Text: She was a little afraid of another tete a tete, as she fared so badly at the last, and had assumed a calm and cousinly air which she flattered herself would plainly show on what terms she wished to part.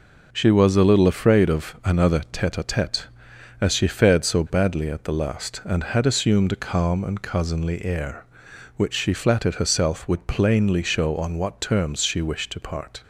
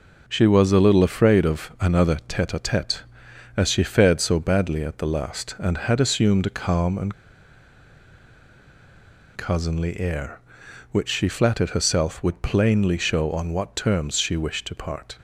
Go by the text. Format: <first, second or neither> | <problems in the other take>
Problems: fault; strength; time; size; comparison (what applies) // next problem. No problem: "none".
first | pauses between "and" and "cousinly"; strong; at 7.1 s; 2.2 s long